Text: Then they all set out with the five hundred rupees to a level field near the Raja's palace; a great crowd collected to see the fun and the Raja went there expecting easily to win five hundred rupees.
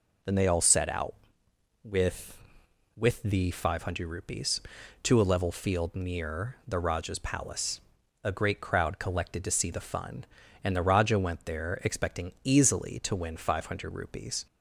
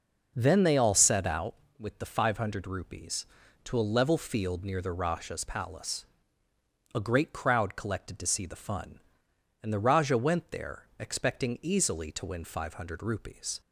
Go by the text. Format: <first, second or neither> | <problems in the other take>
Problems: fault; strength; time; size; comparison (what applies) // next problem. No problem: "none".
second | says "with" twice; at 2.9 s